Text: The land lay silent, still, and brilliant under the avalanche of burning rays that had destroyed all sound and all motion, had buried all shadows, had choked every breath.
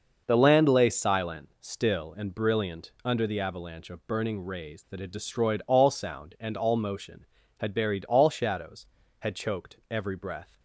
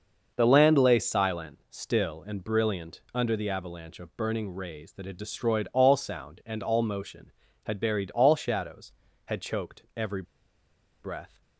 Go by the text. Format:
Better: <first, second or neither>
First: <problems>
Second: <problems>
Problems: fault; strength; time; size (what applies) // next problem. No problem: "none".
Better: first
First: starts louder than the rest; until 1.2 s; 6 dB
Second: starts louder than the rest; until 1.3 s; 6 dB // pauses between "every" and "breath"; noticeable; at 10.2 s; 0.78 s long